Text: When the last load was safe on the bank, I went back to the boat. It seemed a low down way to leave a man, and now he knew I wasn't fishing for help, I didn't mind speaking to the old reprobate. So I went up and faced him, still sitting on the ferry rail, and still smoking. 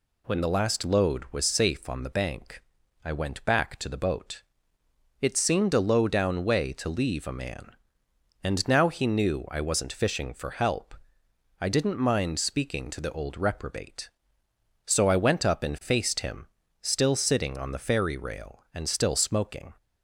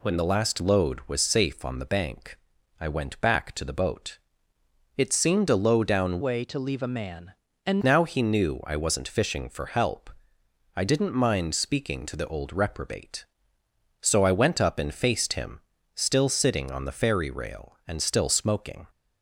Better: first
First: none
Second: changes voice from "way" to "and"; from 6.2 to 7.8 s; 1.6 s long

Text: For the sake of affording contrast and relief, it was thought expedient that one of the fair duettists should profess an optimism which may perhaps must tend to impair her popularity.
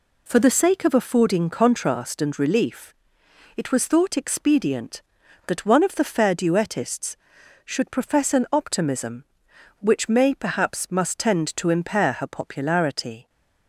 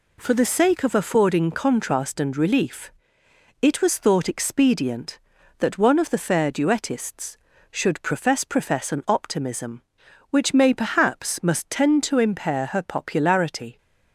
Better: first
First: none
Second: says "profess" twice; at 8.4 s

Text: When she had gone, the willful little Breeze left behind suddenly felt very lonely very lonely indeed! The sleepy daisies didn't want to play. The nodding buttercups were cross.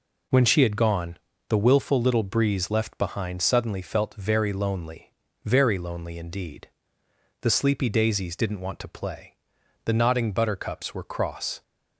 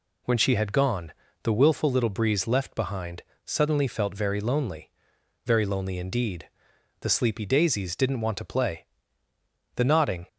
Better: first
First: pauses between "lonely" and "very"; at 5.0 s; 0.38 s long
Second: pauses between "behind" and "suddenly"; slight; at 3.2 s; 0.22 s long // pauses between "lonely" and "very"; noticeable; at 4.8 s; 0.56 s long // stops before "buttercups were cross"; at 10.2 s

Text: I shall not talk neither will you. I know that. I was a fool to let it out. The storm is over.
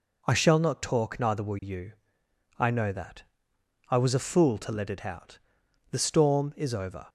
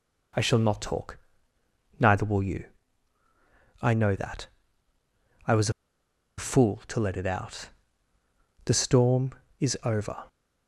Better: first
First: none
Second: pauses between "talk" and "neither"; noticeable; at 1.1 s; 0.82 s long // pauses between "was" and "a"; noticeable; at 5.7 s; 0.67 s long

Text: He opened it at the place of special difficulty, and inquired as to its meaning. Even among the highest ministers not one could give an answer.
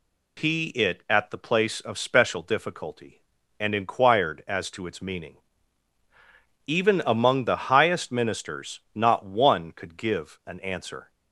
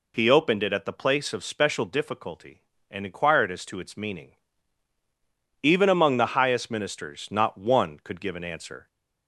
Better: second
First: skips "opened"; at 0.6 s // pauses between "ministers" and "not"; slight; at 8.7 s; 0.16 s long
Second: none

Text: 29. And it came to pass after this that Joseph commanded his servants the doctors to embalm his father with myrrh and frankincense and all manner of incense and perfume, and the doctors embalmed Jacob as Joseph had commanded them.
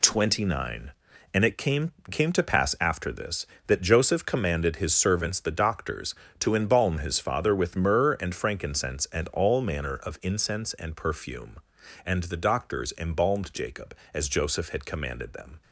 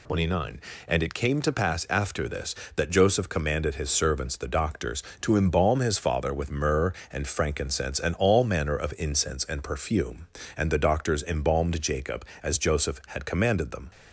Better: second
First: says "came" twice; at 2.0 s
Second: none

